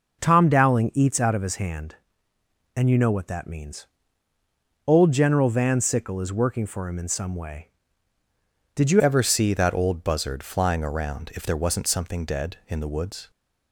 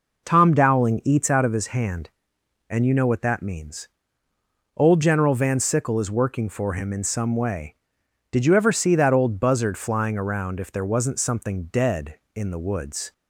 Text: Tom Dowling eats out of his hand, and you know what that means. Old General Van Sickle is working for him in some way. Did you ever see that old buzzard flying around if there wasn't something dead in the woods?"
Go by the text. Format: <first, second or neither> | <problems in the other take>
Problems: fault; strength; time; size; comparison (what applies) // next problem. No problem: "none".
second | changes voice at "ever"; from 9.0 s on; 4.3 s long